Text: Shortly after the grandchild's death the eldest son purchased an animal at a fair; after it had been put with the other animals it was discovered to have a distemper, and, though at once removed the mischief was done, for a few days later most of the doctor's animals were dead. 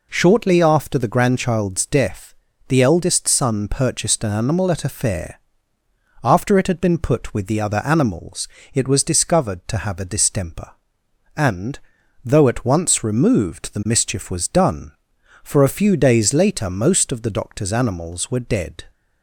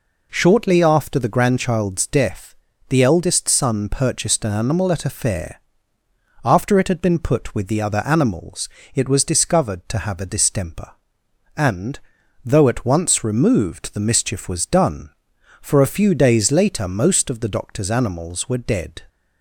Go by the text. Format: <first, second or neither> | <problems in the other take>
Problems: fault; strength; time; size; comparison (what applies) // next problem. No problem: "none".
neither | pauses between "death" and "the"; slight; the same in both // pauses between "animals" and "it"; slight; the same in both